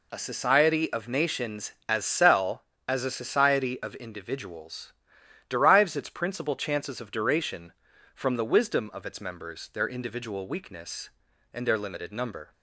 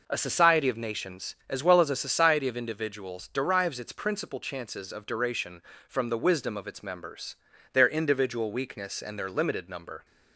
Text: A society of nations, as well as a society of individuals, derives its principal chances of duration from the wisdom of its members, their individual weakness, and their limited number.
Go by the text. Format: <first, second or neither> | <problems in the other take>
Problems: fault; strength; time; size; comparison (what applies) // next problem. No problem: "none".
second | says "cell" for "well"; at 2.0 s